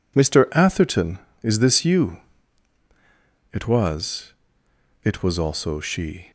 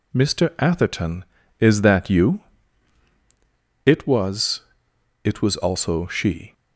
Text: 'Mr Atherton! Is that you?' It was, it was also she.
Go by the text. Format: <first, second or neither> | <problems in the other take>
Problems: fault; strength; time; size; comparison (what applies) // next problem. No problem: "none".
second | says "this" for "that"; at 1.5 s